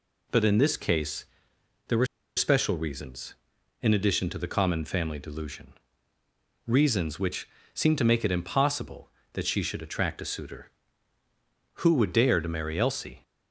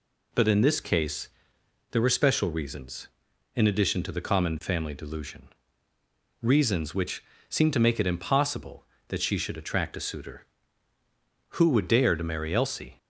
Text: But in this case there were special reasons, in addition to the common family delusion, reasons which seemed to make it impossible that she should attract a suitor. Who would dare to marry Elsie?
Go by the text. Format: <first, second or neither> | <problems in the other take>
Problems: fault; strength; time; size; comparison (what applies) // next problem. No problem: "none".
second | pauses between "case" and "there"; noticeable; at 1.2 s; 0.64 s long; noticeable in the second // pauses between "were" and "special"; slight; at 2.0 s; 0.30 s long // pauses between "which" and "seemed"; slight; at 7.4 s; 0.28 s long; slight in the second